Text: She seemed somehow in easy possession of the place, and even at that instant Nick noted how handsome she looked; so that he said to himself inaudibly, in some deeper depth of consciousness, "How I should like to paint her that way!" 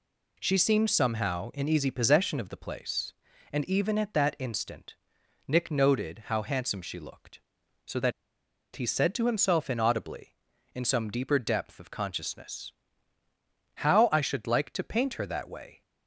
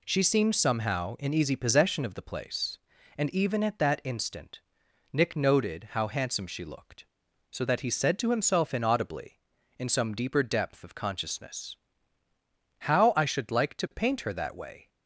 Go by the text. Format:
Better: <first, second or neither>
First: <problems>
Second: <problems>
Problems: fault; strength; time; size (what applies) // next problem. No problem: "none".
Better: second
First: pauses between "instant" and "Nick"; noticeable; at 4.9 s; 0.52 s long // pauses between "that" and "he"; noticeable; at 8.1 s; 0.64 s long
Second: pauses between "instant" and "Nick"; noticeable; at 4.6 s; 0.52 s long